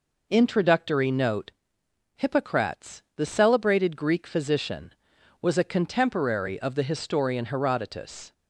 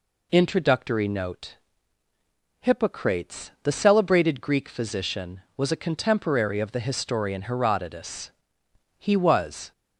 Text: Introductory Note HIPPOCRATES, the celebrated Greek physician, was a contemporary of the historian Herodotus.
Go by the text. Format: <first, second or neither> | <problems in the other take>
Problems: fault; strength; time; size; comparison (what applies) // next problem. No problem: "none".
first | pauses between "Note" and "HIPPOCRATES"; at 1.5 s; 1.0 s long; noticeable in the first // goes on to say "He was"; noticeable; from 8.9 s on; 0.72 s long